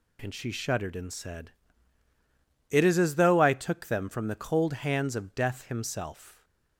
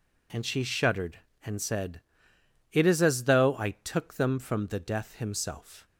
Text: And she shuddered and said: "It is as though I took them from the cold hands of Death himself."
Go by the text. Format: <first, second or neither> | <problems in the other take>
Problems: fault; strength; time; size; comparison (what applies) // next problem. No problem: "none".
first | skips "cold hands of"; at 4.7 s